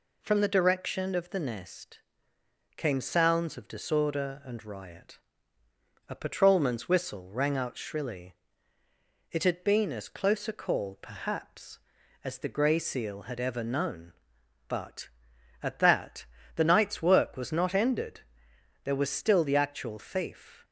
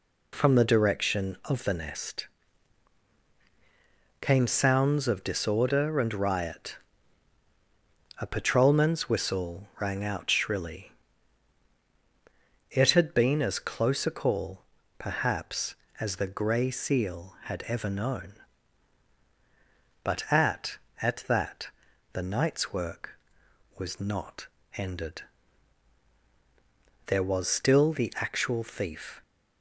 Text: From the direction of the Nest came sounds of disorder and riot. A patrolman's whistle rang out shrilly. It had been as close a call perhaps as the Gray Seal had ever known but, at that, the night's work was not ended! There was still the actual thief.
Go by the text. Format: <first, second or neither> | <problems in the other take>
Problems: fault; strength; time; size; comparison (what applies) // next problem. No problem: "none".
first | pauses between "Nest" and "came"; strong; at 2.2 s; 1.9 s long; noticeable in the first // pauses between "call" and "perhaps"; slight; at 14.6 s; 0.34 s long // says "at" twice; at 20.9 s // pauses between "not" and "ended"; slight; at 24.4 s; 0.28 s long